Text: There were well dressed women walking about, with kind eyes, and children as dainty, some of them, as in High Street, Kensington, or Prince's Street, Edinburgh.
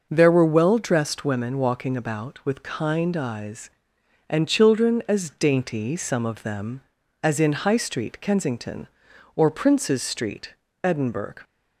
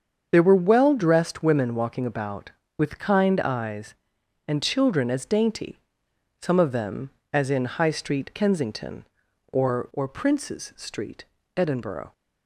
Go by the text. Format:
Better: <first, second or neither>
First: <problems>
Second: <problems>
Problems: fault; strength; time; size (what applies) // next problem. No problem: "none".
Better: first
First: none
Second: starts louder than the rest; strong; until 1.3 s; 7 dB // says "or" twice; at 9.9 s